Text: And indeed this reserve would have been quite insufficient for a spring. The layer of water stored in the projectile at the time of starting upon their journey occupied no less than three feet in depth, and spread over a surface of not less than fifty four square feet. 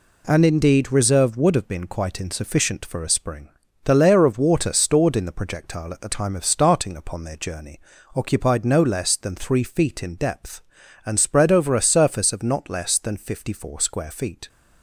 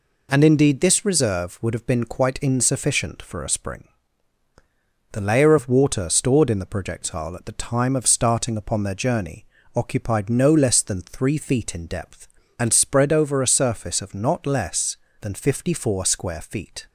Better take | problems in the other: second | skips "this"; at 0.9 s // pauses between "journey" and "occupied"; slight; at 7.7 s; 0.36 s long; slight in the second

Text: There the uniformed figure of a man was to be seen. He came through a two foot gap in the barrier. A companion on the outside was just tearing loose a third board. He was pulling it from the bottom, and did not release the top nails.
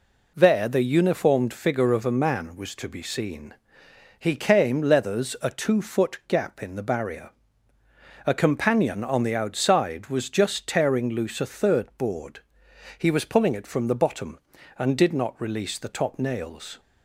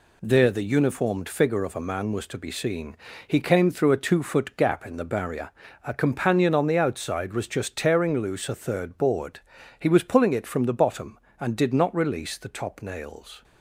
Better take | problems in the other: second | says "leathers" for "through"; at 4.8 s

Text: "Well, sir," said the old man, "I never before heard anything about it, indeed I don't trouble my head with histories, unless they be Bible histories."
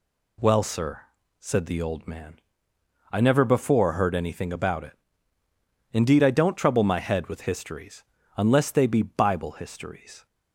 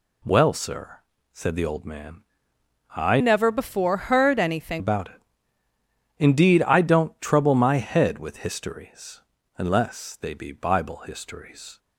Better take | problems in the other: first | changes voice from "never" to "anything"; from 3.1 to 4.8 s; 1.7 s long

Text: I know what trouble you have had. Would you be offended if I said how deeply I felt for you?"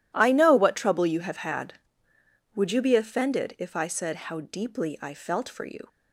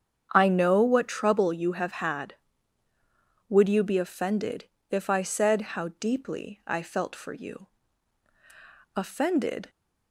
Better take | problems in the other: first | starts louder than the rest; strong; until 1.3 s; 8 dB // pauses between "offended" and "if"; slight; at 4.6 s; 0.24 s long // goes on to say "Offended"; noticeable; from 8.9 s on; 0.76 s long

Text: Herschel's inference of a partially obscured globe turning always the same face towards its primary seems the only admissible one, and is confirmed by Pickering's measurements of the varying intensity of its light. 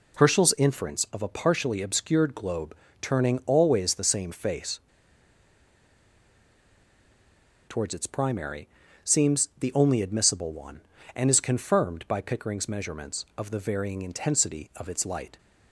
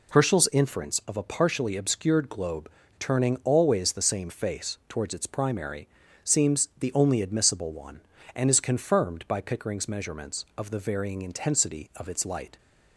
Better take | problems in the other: second | pauses between "globe" and "turning"; slight; at 2.7 s; 0.28 s long; slight in the second // pauses between "face" and "towards"; strong; at 4.7 s; 2.8 s long // pauses between "primary" and "seems"; slight; at 8.6 s; 0.36 s long; slight in the second

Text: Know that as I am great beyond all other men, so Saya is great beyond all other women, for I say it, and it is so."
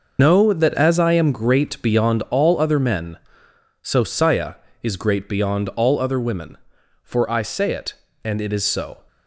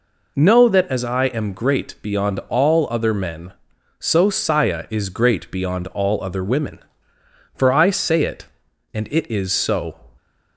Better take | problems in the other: second | loses the start of "Know"; at 0.1 s; 85 ms

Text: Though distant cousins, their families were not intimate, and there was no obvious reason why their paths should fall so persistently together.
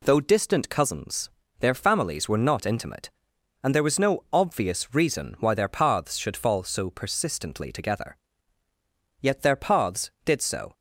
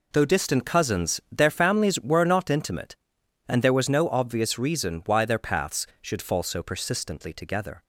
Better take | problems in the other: second | goes on to say "Yet their paths did so"; from 9.2 s on; 1.5 s long

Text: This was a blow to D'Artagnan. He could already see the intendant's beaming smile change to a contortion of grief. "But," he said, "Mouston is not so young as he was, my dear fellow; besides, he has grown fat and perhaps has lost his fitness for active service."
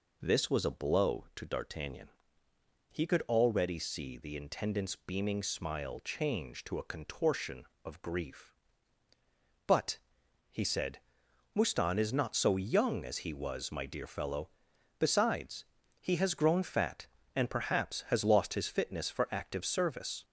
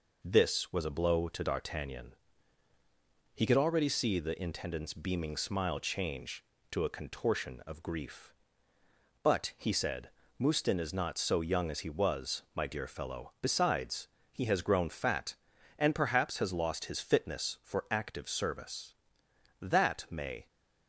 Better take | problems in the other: first | goes on to say "That may"; noticeable; from 19.6 s on; 0.86 s long

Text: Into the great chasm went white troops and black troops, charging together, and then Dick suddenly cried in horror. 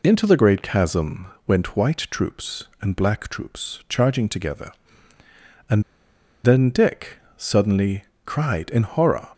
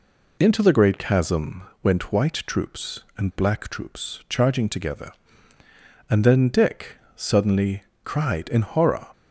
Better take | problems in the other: second | pauses between "chasm" and "went"; slight; at 1.2 s; 0.18 s long; slight in the second // pauses between "and" and "then"; noticeable; at 5.8 s; 0.62 s long // pauses between "Dick" and "suddenly"; slight; at 7.1 s; 0.18 s long; slight in the second // pauses between "suddenly" and "cried"; slight; at 8.0 s; 0.20 s long; slight in the second

